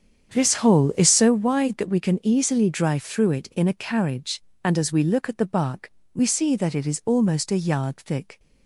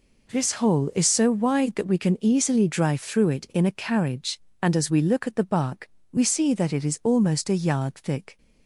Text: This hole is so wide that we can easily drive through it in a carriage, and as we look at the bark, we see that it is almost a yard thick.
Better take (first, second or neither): second